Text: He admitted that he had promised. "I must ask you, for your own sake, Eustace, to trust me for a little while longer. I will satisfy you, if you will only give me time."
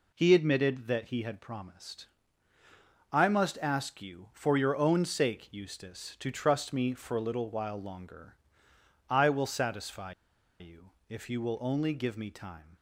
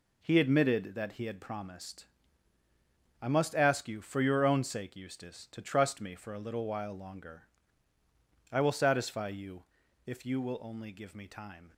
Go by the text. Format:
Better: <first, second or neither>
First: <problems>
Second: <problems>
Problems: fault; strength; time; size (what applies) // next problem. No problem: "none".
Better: second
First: pauses between "satisfy" and "you"; noticeable; at 10.1 s; 0.48 s long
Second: none